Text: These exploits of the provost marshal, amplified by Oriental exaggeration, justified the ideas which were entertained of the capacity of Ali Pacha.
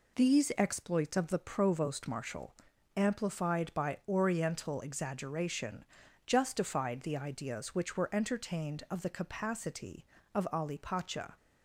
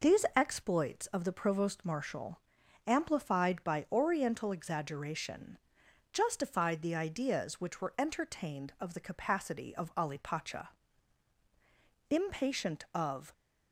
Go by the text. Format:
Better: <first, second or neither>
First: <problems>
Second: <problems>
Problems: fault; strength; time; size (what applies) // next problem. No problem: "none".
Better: first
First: none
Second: goes on to say "Impatient of"; noticeable; from 12.0 s on; 1.2 s long